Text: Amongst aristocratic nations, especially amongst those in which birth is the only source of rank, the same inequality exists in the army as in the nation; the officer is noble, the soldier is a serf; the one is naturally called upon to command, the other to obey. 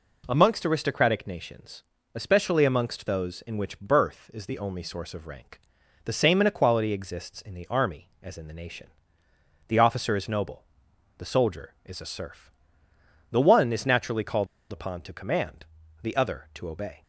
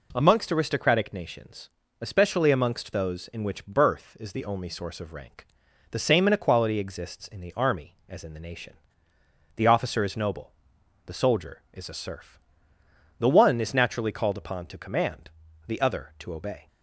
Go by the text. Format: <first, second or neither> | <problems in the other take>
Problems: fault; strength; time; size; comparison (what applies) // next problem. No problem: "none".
second | pauses between "called" and "upon"; slight; at 14.4 s; 0.25 s long